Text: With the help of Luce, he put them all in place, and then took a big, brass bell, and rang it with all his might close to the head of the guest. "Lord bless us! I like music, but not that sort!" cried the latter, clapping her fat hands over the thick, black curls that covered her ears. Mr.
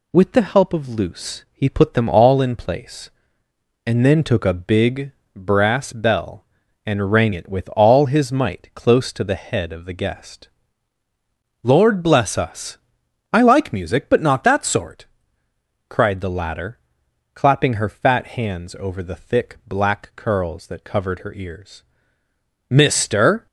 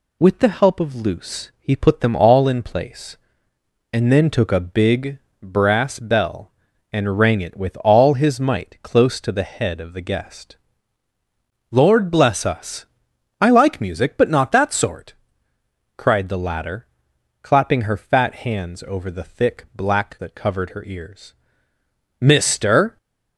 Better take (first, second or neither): first